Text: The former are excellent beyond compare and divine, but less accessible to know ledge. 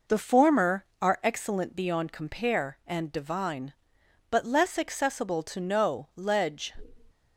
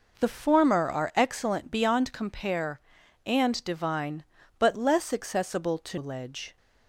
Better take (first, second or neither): first